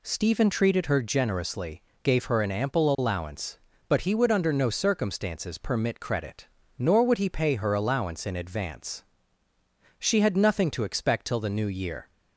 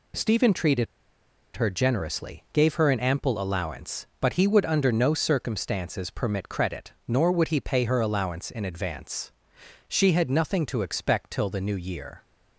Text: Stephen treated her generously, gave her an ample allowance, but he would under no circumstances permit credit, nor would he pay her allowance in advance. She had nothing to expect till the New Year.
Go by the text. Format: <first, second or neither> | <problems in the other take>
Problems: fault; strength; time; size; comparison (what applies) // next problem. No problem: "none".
first | pauses between "treated" and "her"; noticeable; at 0.8 s; 0.70 s long